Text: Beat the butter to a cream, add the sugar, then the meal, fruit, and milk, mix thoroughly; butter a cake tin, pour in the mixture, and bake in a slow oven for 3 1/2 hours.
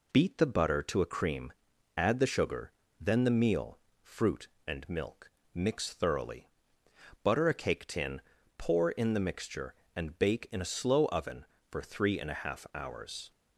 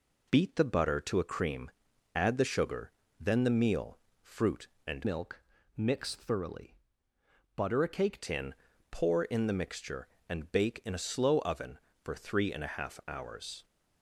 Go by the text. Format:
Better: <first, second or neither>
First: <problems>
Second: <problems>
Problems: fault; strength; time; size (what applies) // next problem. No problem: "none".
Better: first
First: none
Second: changes voice from "milk" to "cake"; from 5.0 to 8.2 s; 3.2 s long